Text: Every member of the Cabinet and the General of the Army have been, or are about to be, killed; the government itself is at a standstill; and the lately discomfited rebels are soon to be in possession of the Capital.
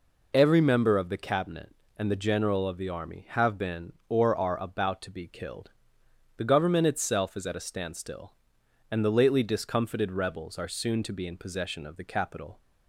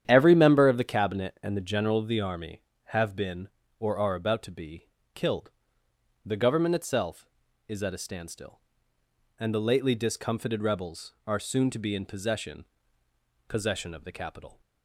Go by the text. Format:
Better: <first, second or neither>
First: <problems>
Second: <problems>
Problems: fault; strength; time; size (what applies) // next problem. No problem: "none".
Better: first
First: none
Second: starts louder than the rest; strong; until 1.0 s; 9.5 dB // says "possession" twice; at 13.4 s